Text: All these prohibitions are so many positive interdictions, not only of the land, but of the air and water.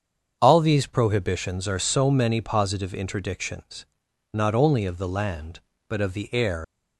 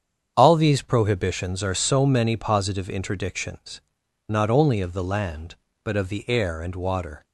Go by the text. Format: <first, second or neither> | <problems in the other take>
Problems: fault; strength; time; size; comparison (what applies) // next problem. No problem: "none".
second | starts louder than the rest; strong; until 1.4 s; 7.5 dB; strong in the second // stops before "and water"; at 6.6 s